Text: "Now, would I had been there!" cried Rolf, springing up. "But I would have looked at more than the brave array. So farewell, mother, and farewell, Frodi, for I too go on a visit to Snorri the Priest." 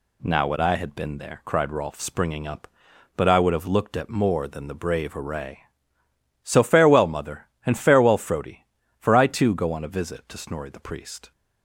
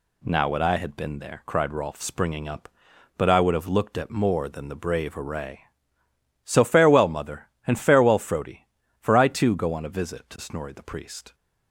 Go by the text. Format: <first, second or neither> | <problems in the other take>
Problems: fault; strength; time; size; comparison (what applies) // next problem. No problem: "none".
neither | none